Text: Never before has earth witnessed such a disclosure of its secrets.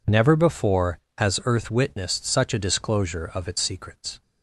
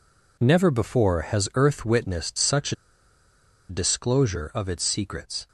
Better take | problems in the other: first | pauses between "a" and "disclosure"; noticeable; at 2.7 s; 0.94 s long

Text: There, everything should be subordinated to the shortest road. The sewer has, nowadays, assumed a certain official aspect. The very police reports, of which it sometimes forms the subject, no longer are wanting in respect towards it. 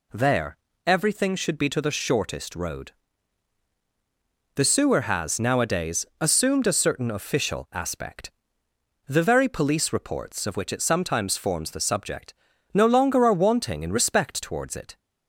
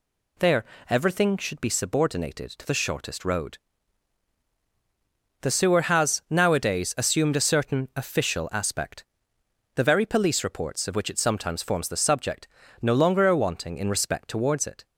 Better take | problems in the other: second | skips "subordinated"; at 1.6 s

